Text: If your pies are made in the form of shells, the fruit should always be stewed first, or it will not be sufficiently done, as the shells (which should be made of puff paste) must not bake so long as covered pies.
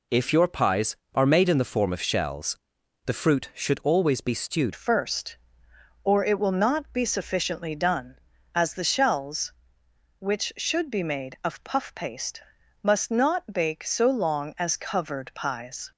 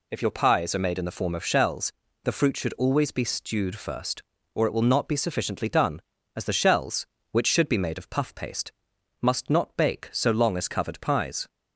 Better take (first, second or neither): second